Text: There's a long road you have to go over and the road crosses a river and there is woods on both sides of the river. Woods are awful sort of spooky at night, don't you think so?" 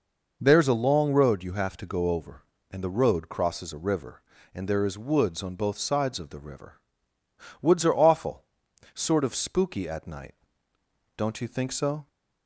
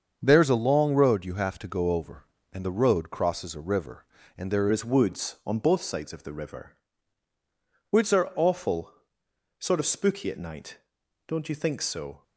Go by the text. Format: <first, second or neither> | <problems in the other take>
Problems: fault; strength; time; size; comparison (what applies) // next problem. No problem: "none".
first | starts louder than the rest; until 1.2 s; 7 dB // changes voice at "is"; from 4.7 s on; 7.5 s long // pauses between "awful" and "sort"; noticeable; at 8.9 s; 0.66 s long; noticeable in the first